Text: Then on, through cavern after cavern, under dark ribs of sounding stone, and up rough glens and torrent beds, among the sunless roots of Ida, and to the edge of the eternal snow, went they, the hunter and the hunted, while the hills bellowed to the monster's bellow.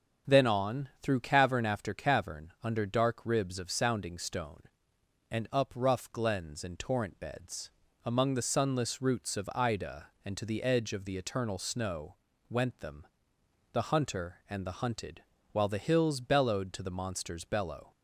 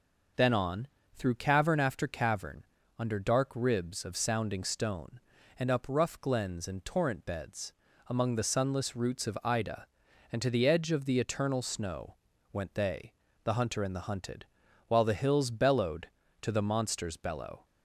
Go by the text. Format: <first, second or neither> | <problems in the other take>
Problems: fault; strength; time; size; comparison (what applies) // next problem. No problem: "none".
second | starts louder than the rest; until 1.3 s; 6.5 dB // says "them" for "they"; at 12.7 s